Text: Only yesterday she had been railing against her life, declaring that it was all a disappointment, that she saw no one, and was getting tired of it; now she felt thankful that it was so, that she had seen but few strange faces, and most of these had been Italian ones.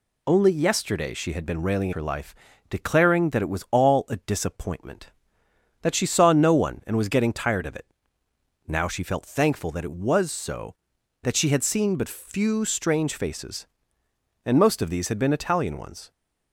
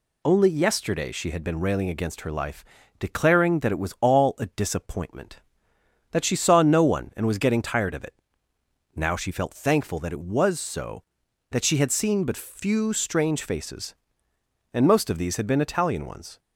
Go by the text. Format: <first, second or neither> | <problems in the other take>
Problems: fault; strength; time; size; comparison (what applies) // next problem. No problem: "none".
second | skips "against"; at 1.9 s